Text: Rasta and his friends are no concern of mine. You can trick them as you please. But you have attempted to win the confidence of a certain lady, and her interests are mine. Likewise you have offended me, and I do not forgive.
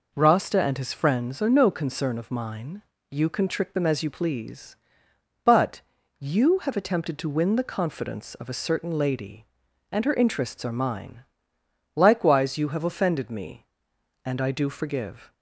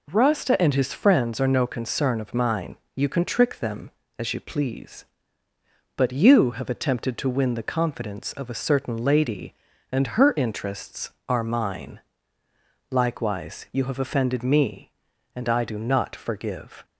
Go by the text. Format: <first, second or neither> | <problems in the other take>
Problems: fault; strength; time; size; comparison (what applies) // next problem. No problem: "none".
second | pauses between "But" and "you"; at 5.8 s; 0.38 s long // skips "not"; at 14.6 s